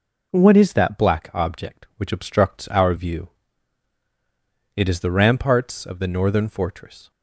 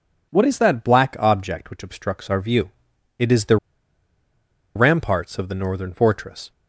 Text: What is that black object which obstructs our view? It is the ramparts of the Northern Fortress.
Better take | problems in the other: first | pauses between "the" and "ramparts"; at 3.5 s; 1.1 s long

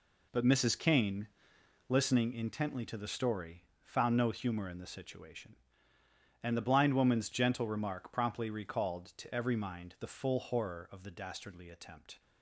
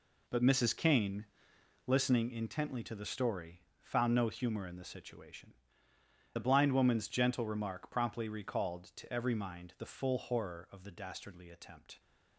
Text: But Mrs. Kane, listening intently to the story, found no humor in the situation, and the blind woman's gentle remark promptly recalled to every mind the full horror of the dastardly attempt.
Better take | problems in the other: first | skips "and"; at 5.9 s

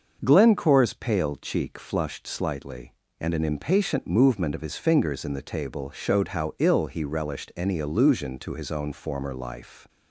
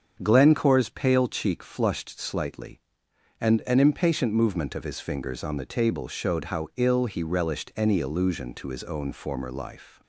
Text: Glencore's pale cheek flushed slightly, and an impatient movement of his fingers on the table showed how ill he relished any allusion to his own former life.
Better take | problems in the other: second | starts louder than the rest; until 1.2 s; 6.5 dB; strong in the second // says "in" for "on"; at 5.2 s

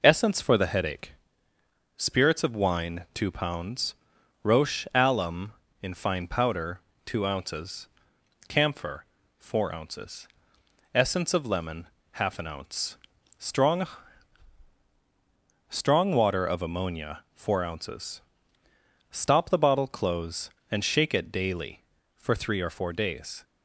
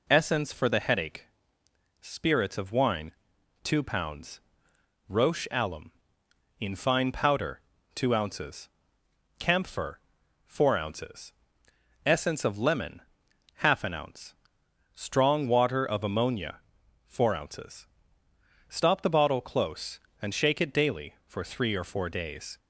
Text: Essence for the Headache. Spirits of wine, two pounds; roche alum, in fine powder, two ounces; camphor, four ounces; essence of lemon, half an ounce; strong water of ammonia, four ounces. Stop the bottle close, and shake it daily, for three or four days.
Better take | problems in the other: second | says "strong" twice; at 15.6 s

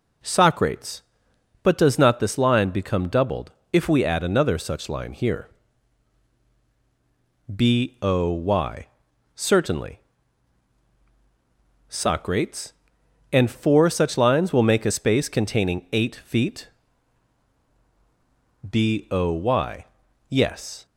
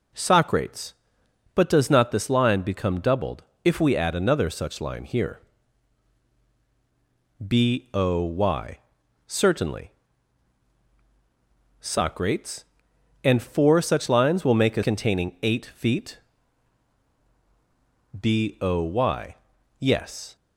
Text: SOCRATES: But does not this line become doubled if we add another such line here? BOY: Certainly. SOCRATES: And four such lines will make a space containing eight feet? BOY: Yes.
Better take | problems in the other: first | pauses between "doubled" and "if"; slight; at 3.4 s; 0.22 s long; slight in the first // skips "space"; at 14.8 s

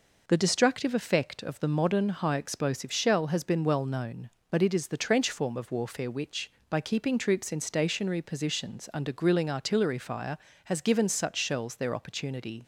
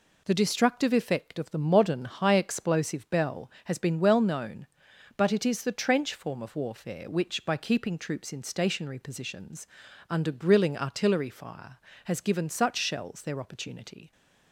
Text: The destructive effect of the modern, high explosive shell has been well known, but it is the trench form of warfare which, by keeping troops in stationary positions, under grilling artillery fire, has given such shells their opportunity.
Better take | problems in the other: first | says "bell" for "shell"; at 3.0 s

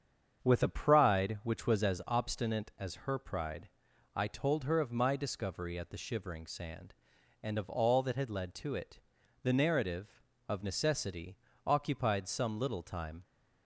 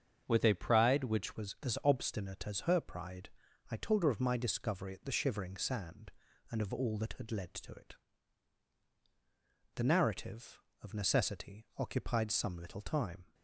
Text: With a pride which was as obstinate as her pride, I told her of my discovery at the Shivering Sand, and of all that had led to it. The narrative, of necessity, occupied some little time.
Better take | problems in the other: first | starts louder than the rest; until 1.2 s; 7 dB; strong in the first // changes voice at "was"; from 1.3 s on; 12.0 s long

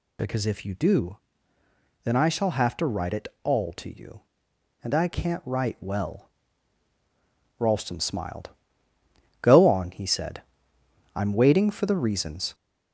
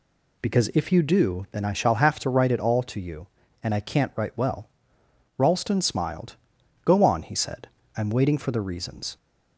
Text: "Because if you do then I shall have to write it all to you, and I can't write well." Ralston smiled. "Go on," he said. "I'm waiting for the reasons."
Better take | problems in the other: second | gets louder; throughout; 3.5 dB // pauses between "do" and "then"; noticeable; at 1.1 s; 0.86 s long

